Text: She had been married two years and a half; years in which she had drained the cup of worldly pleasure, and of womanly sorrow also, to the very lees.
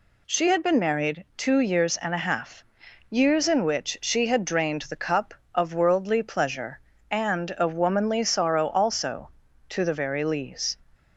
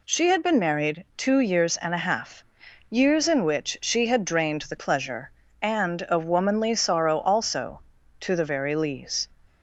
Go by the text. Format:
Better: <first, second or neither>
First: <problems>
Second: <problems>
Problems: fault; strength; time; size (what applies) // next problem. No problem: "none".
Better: first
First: none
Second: skips "cup of worldly"; at 4.7 s